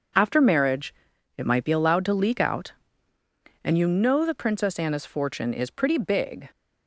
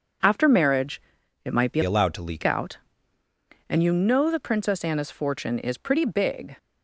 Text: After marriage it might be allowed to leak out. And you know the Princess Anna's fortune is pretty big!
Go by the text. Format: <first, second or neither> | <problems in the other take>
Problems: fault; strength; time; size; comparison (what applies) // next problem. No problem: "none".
first | pauses between "marriage" and "it"; at 1.0 s; 0.44 s long; also in the first // changes voice from "allowed" to "leak"; from 1.8 to 2.4 s; 0.6 s long